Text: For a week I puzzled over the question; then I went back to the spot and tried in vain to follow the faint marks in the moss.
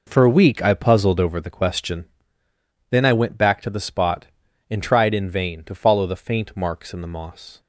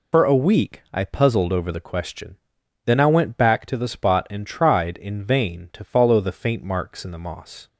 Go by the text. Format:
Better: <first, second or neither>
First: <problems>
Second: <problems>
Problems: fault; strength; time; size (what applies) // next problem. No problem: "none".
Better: first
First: none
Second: loses the start of "For"; at 0.1 s; 45 ms